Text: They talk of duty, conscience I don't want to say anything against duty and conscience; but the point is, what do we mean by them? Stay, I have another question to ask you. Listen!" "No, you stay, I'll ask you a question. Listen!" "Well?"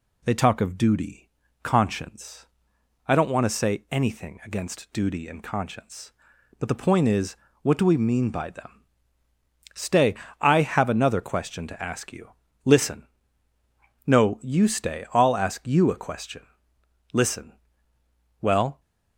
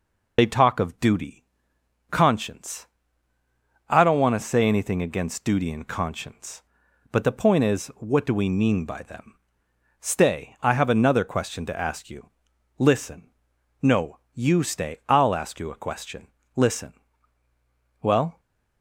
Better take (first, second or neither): first